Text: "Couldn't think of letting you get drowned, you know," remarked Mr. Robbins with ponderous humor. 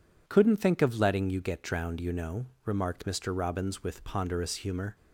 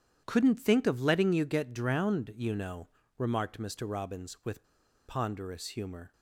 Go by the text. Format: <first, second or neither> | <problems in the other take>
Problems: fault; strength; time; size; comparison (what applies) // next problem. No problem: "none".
first | starts louder than the rest; strong; until 1.2 s; 9.5 dB // pauses between "with" and "ponderous"; at 4.6 s; 0.44 s long